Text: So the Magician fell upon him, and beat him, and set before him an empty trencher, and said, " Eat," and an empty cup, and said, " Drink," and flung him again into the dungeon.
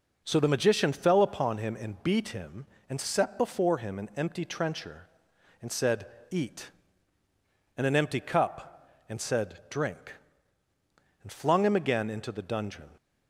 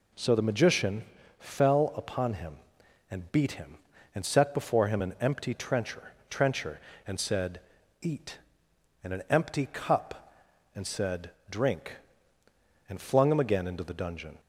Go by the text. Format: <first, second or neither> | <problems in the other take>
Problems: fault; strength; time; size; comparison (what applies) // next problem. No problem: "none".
first | pauses between "Magician" and "fell"; slight; at 1.0 s; 0.34 s long // says "trencher" twice; at 6.2 s